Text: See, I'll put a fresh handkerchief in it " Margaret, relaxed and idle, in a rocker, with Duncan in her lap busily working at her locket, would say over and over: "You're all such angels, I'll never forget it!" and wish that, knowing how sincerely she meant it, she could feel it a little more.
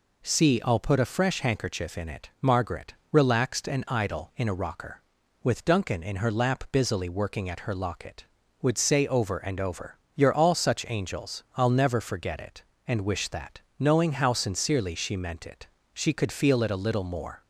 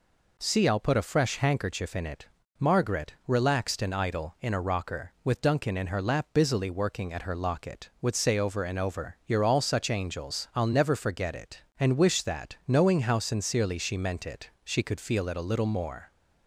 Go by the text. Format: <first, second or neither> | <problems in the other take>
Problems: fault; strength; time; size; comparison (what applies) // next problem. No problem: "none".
neither | none